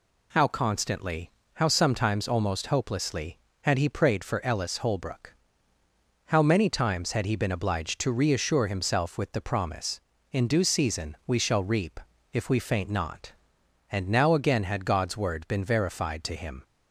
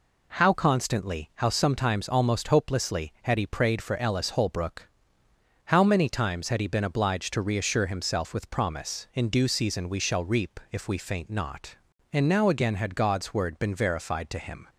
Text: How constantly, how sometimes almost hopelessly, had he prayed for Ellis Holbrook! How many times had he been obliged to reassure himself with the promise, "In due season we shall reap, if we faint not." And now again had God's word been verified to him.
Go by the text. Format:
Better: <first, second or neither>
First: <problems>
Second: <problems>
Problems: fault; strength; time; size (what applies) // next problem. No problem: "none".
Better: first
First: none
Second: skips "the"; at 8.4 s